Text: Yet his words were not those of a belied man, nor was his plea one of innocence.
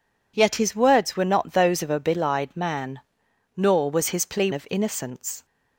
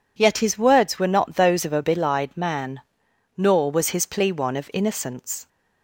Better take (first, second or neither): second